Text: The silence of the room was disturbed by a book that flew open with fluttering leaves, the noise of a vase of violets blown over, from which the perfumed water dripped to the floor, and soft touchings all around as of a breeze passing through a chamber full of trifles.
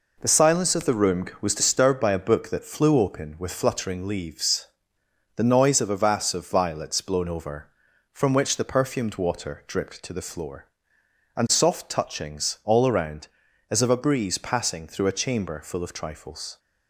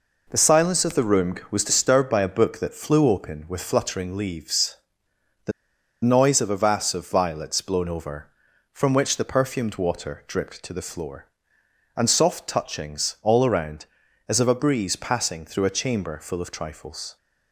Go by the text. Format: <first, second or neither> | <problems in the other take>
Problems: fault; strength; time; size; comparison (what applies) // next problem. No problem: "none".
first | pauses between "the" and "noise"; noticeable; at 5.5 s; 0.53 s long